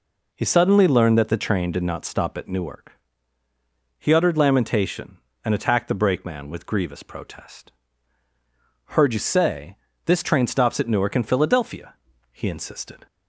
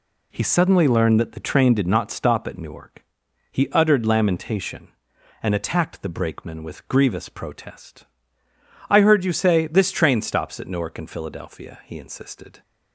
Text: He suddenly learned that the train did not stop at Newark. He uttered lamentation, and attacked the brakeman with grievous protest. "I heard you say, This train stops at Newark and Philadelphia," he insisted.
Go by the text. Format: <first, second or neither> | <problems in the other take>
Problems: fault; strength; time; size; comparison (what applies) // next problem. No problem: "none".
second | skips "I"; at 8.3 s